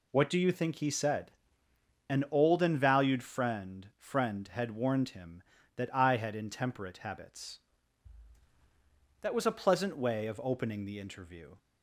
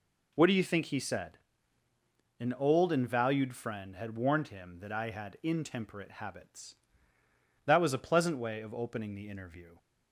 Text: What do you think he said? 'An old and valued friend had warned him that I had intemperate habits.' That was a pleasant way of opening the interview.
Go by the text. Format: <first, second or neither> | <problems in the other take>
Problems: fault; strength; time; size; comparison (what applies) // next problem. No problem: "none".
second | says "friend" twice; at 3.9 s